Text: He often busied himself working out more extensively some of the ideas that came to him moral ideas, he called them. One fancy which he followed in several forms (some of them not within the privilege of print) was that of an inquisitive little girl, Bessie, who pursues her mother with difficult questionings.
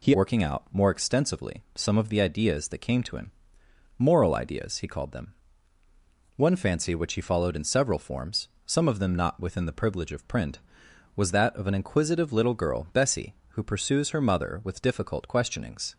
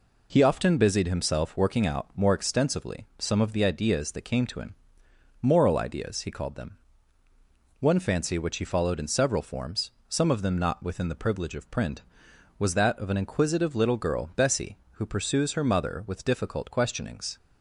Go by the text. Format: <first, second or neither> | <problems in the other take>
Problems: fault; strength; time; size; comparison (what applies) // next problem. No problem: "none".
second | skips "often busied himself"; at 0.1 s // pauses between "him" and "moral"; noticeable; at 3.3 s; 0.66 s long; noticeable in the second